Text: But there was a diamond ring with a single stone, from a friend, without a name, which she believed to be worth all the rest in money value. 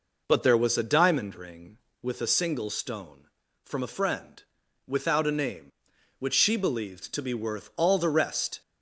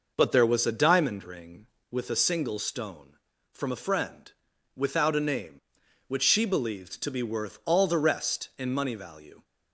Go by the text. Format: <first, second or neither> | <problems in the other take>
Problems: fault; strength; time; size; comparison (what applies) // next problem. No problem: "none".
second | stops before "in money value"; at 8.6 s